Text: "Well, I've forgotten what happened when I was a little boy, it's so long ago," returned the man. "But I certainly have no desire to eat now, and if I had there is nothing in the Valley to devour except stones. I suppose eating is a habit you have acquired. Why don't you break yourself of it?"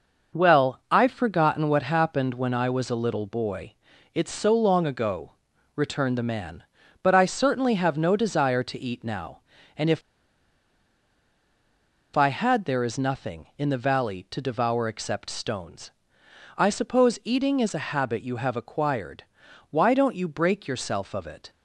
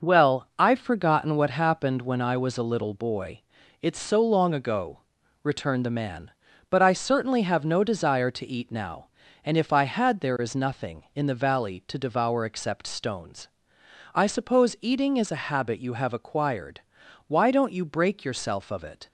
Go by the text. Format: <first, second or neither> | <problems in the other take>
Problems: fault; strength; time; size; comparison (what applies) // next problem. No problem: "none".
second | pauses between "if" and "I"; strong; at 10.0 s; 2.1 s long